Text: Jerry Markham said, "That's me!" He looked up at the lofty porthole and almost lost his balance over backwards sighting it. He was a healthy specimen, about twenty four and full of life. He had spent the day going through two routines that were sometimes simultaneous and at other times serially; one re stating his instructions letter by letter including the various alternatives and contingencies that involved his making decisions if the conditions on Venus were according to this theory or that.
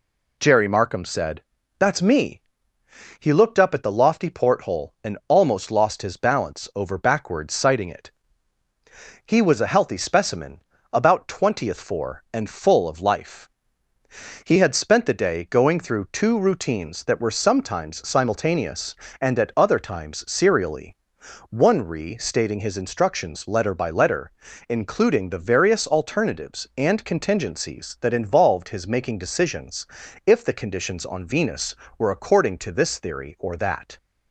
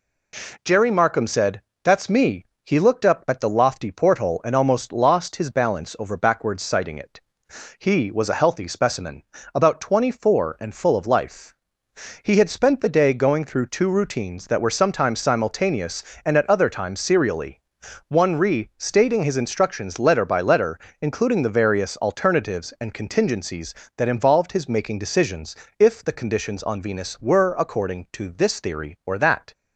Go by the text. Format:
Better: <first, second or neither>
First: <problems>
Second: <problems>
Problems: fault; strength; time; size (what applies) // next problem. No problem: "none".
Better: second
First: says "twentieth" for "twenty"; at 11.2 s // pauses between "letter" and "including"; at 24.3 s; 0.38 s long // pauses between "decisions" and "if"; at 29.8 s; 0.40 s long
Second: pauses between "letter" and "including"; slight; at 20.8 s; 0.20 s long // pauses between "decisions" and "if"; slight; at 25.5 s; 0.24 s long